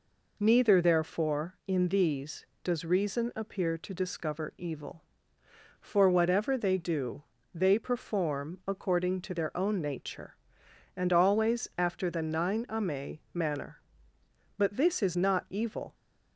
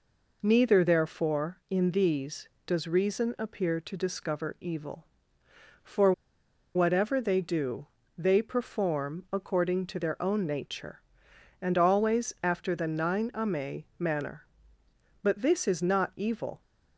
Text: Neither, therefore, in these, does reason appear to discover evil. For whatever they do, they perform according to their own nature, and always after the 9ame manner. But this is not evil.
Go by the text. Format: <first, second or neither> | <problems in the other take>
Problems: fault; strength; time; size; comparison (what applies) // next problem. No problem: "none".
first | pauses between "For" and "whatever"; noticeable; at 6.1 s; 0.63 s long